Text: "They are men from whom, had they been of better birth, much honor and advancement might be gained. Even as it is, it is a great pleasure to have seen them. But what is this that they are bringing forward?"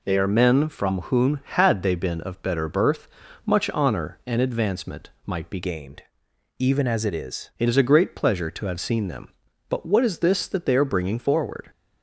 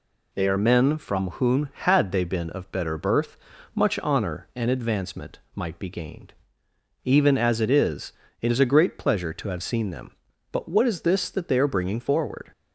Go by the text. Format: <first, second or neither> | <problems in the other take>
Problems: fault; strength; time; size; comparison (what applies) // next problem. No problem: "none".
second | pauses between "advancement" and "might"; slight; at 5.0 s; 0.18 s long; slight in the second // changes voice from "gained" to "is"; from 5.6 to 7.4 s; 1.8 s long